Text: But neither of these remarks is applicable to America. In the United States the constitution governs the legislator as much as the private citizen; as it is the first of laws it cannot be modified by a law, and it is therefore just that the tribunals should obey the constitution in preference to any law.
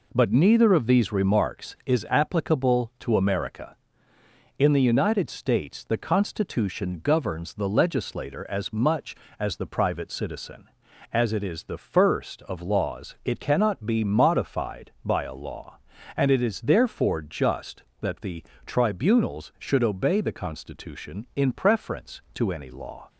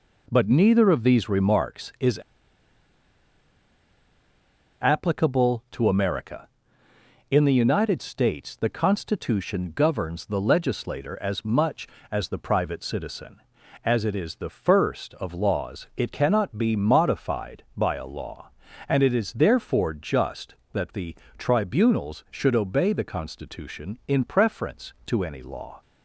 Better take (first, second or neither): first